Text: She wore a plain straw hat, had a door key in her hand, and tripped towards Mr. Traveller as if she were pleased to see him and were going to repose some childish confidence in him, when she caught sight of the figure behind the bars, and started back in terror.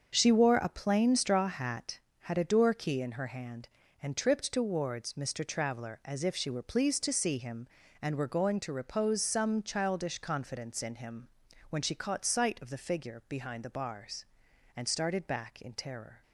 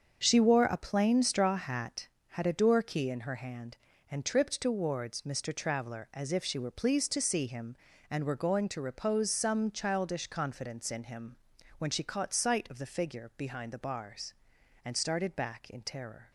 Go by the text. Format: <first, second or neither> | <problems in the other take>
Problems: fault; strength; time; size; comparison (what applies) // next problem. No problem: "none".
neither | starts louder than the rest; the same in both